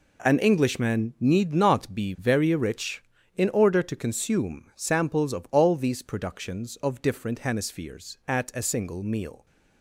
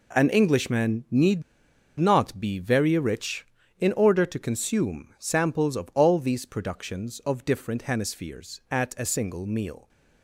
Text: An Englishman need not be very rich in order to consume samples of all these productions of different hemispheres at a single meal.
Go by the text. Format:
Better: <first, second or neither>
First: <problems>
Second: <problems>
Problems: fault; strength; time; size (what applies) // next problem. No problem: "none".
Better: first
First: none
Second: pauses between "need" and "not"; noticeable; at 1.4 s; 0.57 s long